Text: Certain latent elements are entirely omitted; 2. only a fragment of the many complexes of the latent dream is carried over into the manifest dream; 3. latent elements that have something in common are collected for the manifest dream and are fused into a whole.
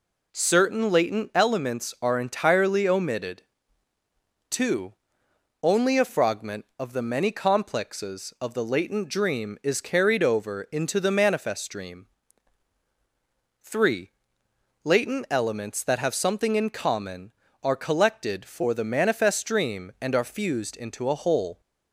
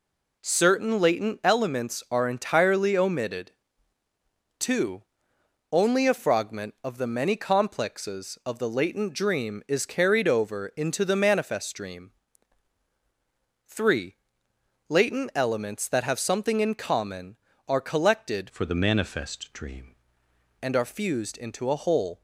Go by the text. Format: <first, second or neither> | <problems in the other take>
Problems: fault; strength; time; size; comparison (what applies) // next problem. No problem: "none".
first | changes voice from "for" to "dream"; from 18.4 to 19.9 s; 1.5 s long